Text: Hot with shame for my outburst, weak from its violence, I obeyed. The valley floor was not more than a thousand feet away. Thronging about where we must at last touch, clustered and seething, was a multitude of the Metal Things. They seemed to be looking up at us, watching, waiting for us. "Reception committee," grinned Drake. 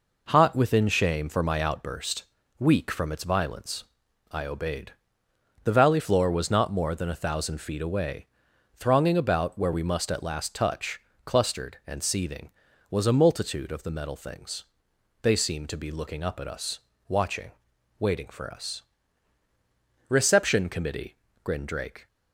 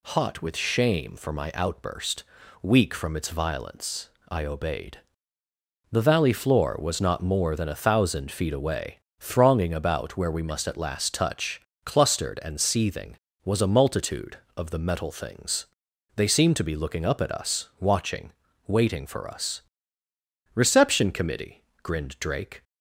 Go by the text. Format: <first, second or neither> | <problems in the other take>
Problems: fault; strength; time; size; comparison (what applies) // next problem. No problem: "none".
second | says "within" for "with"; at 0.5 s